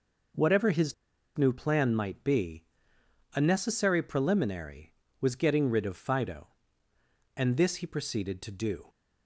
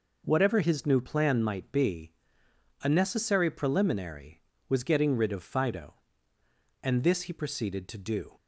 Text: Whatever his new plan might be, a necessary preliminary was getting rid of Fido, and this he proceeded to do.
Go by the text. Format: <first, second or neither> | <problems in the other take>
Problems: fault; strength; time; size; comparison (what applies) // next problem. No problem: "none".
second | pauses between "his" and "new"; at 0.9 s; 0.43 s long